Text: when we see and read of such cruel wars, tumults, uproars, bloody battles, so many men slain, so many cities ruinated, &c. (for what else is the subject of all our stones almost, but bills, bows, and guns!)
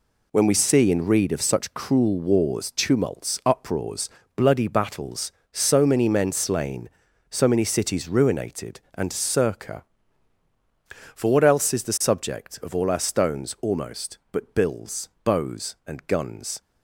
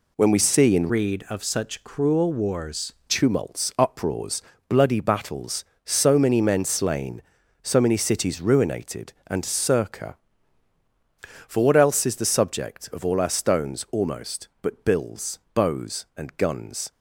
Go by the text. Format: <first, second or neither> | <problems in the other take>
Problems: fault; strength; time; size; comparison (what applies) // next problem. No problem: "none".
first | changes voice from "read" to "wars"; from 0.8 to 2.9 s; 2.1 s long